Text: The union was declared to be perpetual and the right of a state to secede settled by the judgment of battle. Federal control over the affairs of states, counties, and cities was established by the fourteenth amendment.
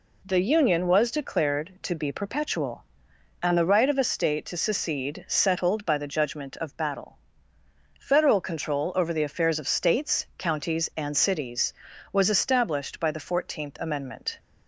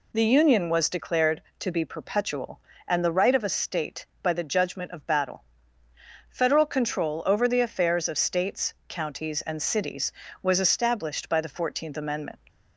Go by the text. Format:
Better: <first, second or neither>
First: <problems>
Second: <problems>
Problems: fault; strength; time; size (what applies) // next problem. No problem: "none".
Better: first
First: none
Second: skips "to secede settled"; at 4.1 s